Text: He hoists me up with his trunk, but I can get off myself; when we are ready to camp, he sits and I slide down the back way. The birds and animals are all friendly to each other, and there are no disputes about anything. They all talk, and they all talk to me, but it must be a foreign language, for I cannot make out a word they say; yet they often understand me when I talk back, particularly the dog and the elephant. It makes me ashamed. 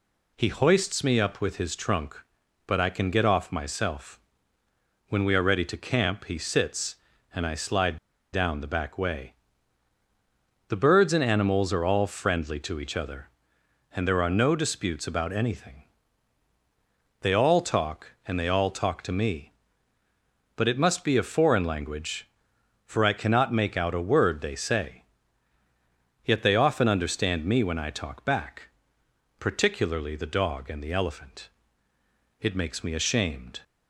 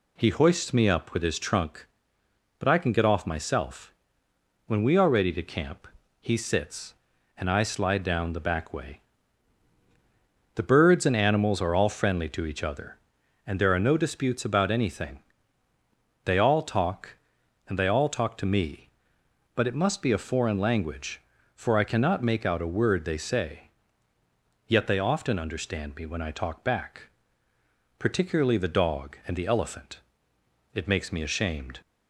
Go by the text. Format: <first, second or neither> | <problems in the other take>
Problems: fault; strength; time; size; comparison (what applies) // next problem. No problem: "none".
second | pauses between "slide" and "down"; slight; at 7.9 s; 0.36 s long